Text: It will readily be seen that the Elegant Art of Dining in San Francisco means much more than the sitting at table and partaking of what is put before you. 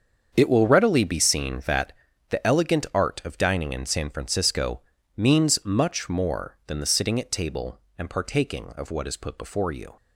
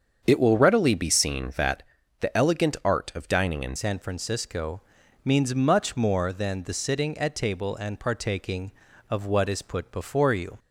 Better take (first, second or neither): first